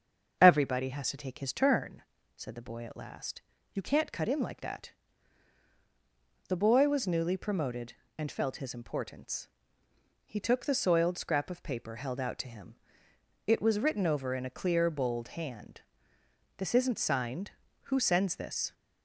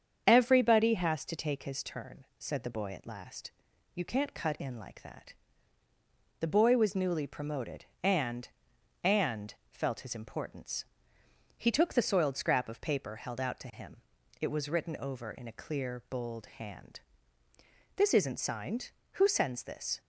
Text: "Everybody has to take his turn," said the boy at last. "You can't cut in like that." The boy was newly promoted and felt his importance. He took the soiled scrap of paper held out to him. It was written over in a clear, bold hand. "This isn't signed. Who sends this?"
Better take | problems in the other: first | starts louder than the rest; strong; until 1.2 s; 7.5 dB; also in the first // says "and" twice; at 9.0 s

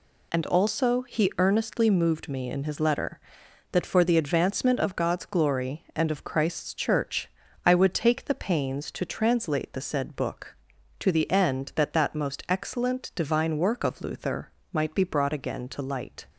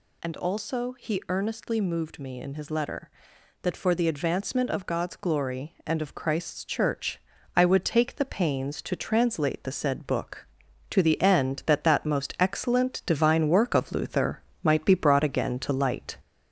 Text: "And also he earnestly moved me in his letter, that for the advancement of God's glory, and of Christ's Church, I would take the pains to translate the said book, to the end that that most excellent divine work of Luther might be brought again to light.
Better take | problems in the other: first | gets louder; throughout; 3.5 dB // pauses between "Luther" and "might"; slight; at 14.4 s; 0.22 s long; slight in the first

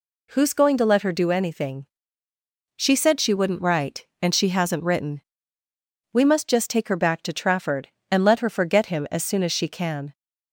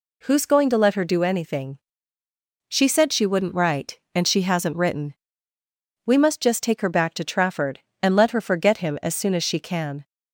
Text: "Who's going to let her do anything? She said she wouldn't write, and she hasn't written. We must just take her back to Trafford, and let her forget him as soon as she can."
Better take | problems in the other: neither | none

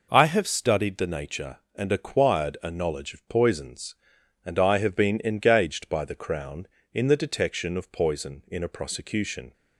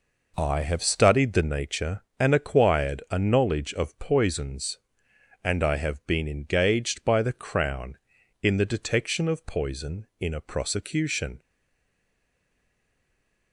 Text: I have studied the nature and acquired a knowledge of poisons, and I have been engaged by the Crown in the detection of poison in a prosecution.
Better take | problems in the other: first | stays silent after the last word; from 11.3 s on; 2.2 s long

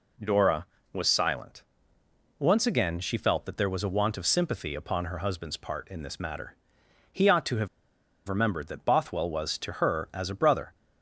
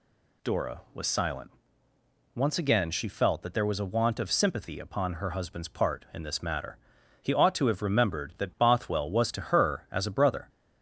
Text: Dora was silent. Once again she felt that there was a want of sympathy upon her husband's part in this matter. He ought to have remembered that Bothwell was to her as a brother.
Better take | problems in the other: second | pauses between "have" and "remembered"; noticeable; at 7.6 s; 0.60 s long

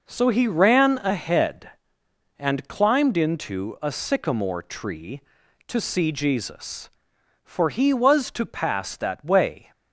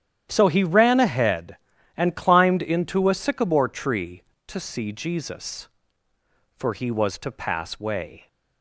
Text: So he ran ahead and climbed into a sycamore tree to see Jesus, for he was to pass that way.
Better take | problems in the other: first | starts louder than the rest; strong; until 1.3 s; 10.5 dB // skips "that"; at 7.7 s

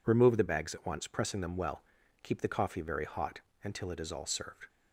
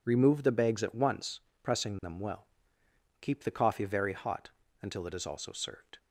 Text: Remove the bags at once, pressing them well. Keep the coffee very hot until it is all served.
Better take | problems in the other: first | pauses between "hot" and "until"; slight; at 4.4 s; 0.32 s long; slight in the first // says "also" for "all"; at 5.2 s

